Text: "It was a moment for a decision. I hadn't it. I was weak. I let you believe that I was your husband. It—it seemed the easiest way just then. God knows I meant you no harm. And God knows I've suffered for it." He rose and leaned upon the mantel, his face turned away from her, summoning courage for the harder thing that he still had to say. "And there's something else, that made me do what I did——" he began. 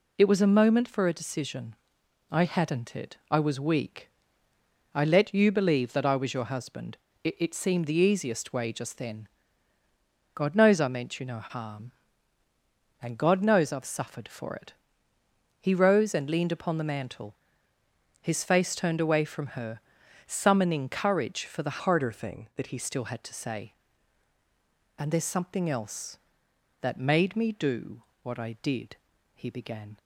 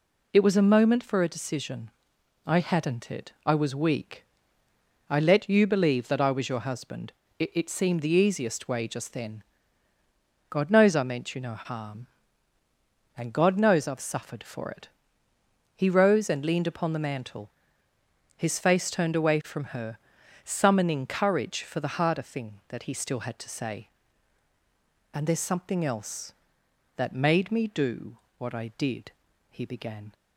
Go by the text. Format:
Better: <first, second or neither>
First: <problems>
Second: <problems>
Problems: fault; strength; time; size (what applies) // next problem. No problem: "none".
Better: second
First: changes voice from "harder" to "he"; from 21.8 to 22.7 s; 0.9 s long // pauses between "do" and "what"; slight; at 28.0 s; 0.20 s long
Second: pauses between "do" and "what"; slight; at 28.1 s; 0.20 s long